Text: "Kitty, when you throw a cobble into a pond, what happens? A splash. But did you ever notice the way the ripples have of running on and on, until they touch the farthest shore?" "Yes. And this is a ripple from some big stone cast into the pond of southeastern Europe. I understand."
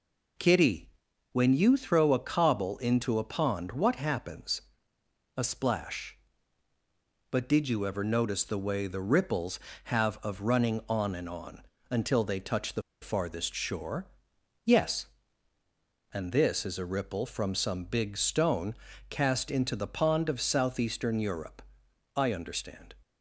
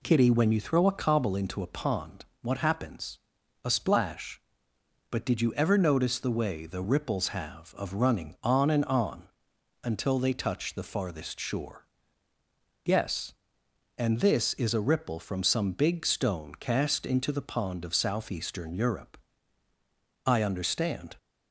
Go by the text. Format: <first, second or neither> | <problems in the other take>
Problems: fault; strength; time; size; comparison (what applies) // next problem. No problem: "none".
second | pauses between "the" and "farthest"; slight; at 12.8 s; 0.20 s long // pauses between "stone" and "cast"; slight; at 18.7 s; 0.34 s long